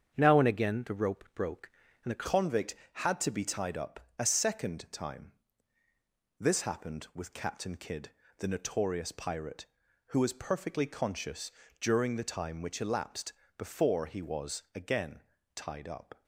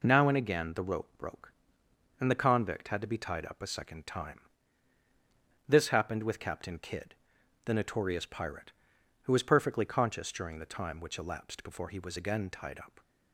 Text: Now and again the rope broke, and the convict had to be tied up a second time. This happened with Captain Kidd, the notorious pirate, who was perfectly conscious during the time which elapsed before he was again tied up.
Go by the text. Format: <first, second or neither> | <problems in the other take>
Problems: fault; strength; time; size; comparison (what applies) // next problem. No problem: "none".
second | starts louder than the rest; strong; until 1.1 s; 8 dB // changes voice at "convict"; from 2.2 s on; 14.0 s long // pauses between "up" and "a"; slight; at 3.9 s; 0.20 s long // pauses between "conscious" and "during"; slight; at 11.4 s; 0.30 s long // pauses between "elapsed" and "before"; slight; at 13.3 s; 0.24 s long // pauses between "again" and "tied"; slight; at 15.2 s; 0.34 s long